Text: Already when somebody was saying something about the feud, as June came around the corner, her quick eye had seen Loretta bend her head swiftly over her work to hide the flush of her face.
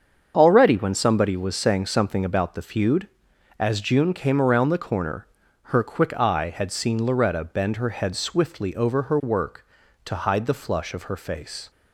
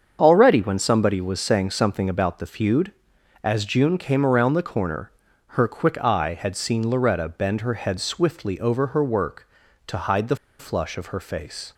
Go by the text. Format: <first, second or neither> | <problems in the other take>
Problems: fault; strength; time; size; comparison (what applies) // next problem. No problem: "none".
first | starts louder than the rest; until 1.2 s; 7 dB; also in the first // pauses between "the" and "flush"; slight; at 10.3 s; 0.23 s long